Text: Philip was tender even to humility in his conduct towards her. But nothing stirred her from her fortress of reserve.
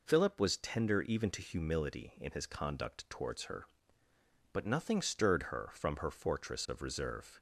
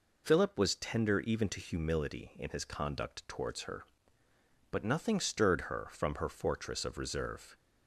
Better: neither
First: none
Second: none

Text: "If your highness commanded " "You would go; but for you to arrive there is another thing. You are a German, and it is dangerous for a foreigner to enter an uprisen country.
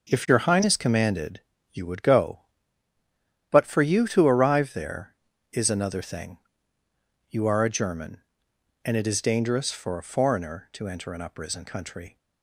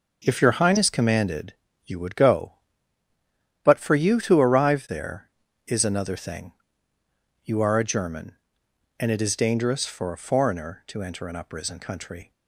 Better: neither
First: none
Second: none

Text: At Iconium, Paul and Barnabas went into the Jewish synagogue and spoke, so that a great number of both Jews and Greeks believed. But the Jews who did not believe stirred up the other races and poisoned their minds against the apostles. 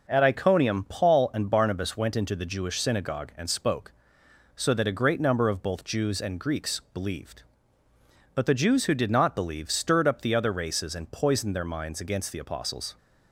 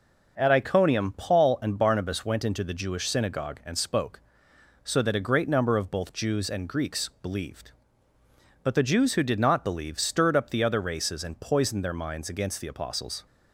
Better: neither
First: none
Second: none

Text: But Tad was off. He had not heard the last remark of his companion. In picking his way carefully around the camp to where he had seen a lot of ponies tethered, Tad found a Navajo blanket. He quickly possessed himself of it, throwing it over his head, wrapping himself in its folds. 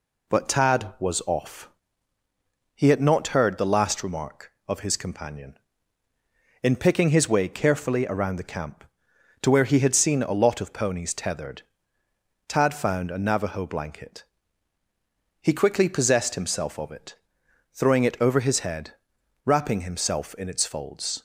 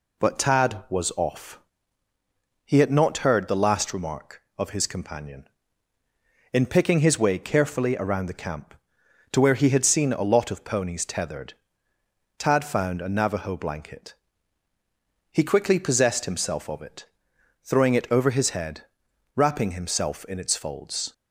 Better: neither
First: none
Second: none

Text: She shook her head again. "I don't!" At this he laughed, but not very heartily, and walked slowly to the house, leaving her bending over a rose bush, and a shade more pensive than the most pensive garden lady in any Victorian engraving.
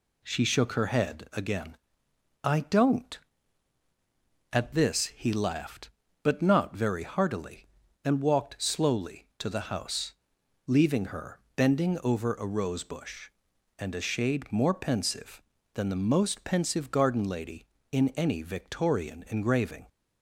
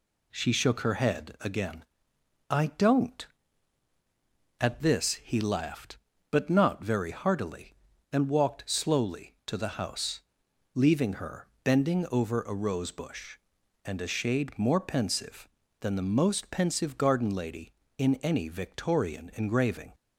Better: neither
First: pauses between "her" and "bending"; slight; at 11.3 s; 0.16 s long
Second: pauses between "her" and "bending"; slight; at 11.4 s; 0.16 s long

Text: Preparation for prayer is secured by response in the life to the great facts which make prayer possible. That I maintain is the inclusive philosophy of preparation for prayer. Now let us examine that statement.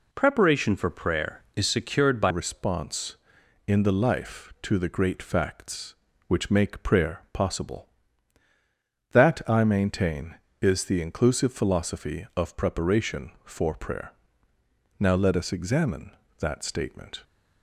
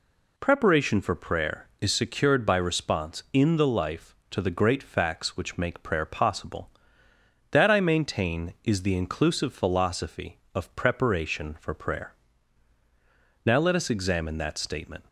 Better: second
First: changes voice at "response"; from 2.2 s on; 15.0 s long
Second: none

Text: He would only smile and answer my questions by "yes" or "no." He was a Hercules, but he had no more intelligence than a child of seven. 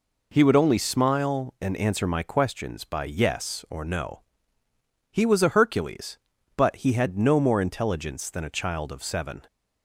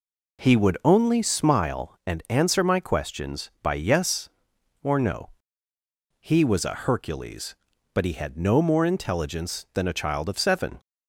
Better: neither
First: none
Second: none

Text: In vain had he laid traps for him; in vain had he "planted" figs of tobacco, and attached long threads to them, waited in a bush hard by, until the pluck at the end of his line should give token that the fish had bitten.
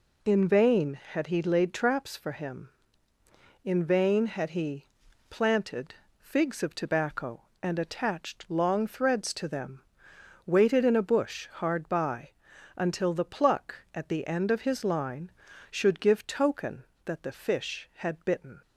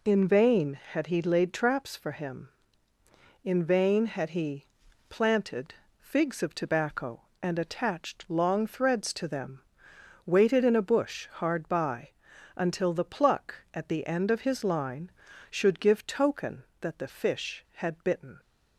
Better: neither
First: pauses between "he" and "planted"; noticeable; at 4.8 s; 0.46 s long // pauses between "planted" and "figs"; slight; at 5.9 s; 0.24 s long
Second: pauses between "he" and "planted"; noticeable; at 4.6 s; 0.46 s long // pauses between "planted" and "figs"; slight; at 5.7 s; 0.24 s long

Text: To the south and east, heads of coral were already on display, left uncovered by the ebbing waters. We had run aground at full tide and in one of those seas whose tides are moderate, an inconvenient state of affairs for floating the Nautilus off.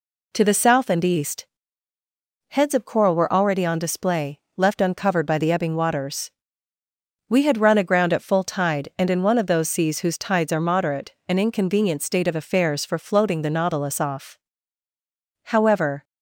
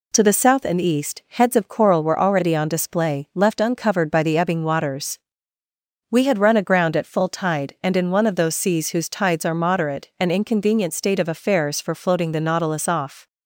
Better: second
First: goes on to say "However"; from 15.4 s on; 0.60 s long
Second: none

